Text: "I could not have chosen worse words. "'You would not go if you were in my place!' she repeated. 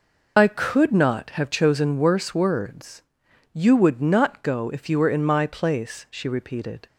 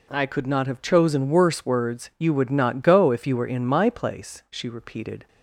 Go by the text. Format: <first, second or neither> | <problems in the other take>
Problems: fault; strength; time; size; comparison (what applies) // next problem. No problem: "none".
second | loses the start of "I"; at 0.3 s; 40 ms